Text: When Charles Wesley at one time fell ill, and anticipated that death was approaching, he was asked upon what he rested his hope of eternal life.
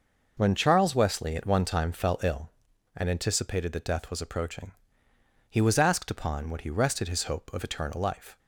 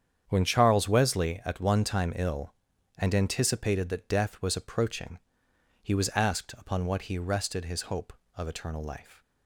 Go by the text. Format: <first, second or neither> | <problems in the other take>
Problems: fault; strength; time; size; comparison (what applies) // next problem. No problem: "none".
first | starts louder than the rest; strong; until 1.2 s; 8.5 dB // skips "fell"; at 2.1 s